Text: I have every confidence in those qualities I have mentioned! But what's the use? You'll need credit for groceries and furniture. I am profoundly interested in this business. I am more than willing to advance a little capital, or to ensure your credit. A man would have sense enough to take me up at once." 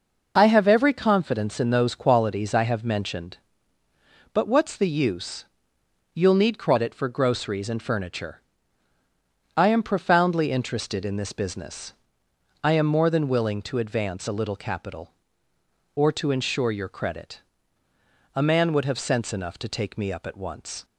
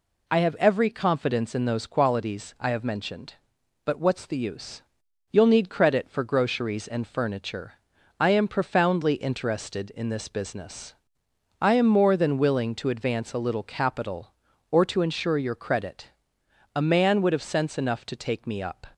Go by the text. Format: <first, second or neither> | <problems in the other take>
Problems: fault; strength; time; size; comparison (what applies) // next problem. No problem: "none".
first | stops before "at once"; at 18.9 s